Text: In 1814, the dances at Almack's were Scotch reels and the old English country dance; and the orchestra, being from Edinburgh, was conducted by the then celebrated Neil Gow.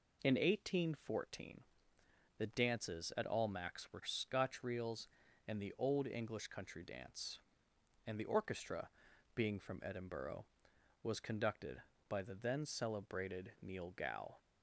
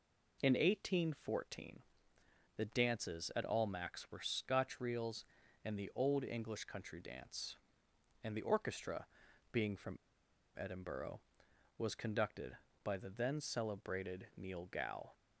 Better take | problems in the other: first | pauses between "from" and "Edinburgh"; noticeable; at 9.9 s; 0.62 s long

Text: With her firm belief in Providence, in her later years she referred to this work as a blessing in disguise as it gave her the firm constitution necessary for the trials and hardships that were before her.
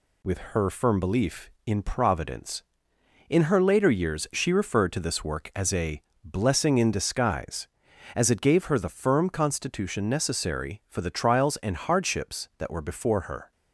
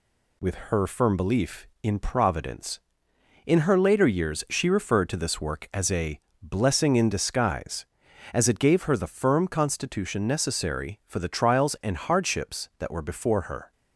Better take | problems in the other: neither | pauses between "a" and "blessing"; slight; the same in both

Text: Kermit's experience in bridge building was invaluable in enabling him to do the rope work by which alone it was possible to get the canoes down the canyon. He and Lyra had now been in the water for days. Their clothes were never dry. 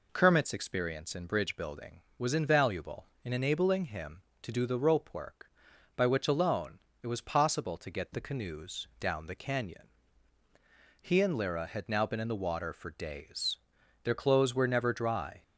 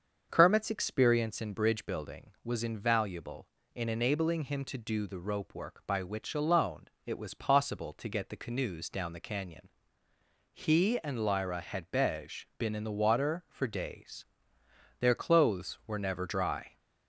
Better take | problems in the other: first | starts louder than the rest; until 1.3 s; 7 dB // pauses between "alone" and "it"; slight; at 6.8 s; 0.18 s long; slight in the first // says "bej" for "now"; at 11.9 s

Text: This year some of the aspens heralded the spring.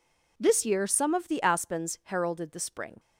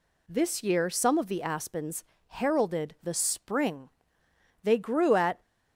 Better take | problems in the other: first | pauses between "aspens" and "heralded"; slight; at 2.0 s; 0.24 s long // goes on to say "They grew at"; noticeable; from 4.6 s on; 0.78 s long

